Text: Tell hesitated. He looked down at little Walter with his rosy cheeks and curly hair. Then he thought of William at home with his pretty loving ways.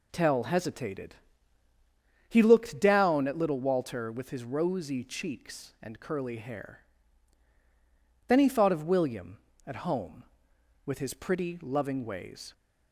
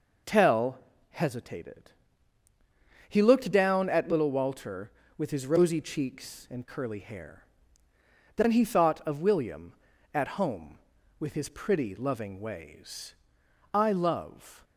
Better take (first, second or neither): first